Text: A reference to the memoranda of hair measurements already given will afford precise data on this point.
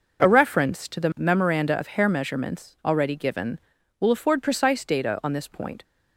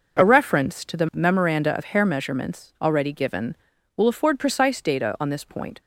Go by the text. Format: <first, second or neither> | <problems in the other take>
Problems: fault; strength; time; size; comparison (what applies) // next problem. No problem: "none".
neither | none